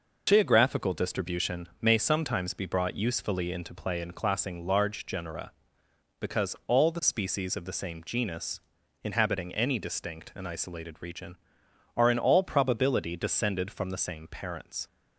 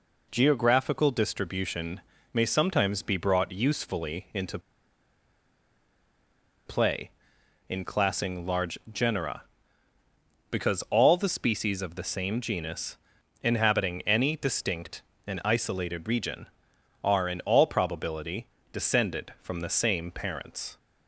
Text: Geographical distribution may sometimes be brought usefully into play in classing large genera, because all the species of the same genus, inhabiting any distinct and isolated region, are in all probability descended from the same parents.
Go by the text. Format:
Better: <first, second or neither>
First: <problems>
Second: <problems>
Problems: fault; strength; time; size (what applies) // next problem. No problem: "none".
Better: first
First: none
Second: pauses between "distribution" and "may"; slight; at 2.0 s; 0.34 s long // pauses between "into" and "play"; strong; at 4.5 s; 2.0 s long // pauses between "large" and "genera"; slight; at 8.7 s; 0.16 s long // pauses between "probability" and "descended"; slight; at 18.4 s; 0.24 s long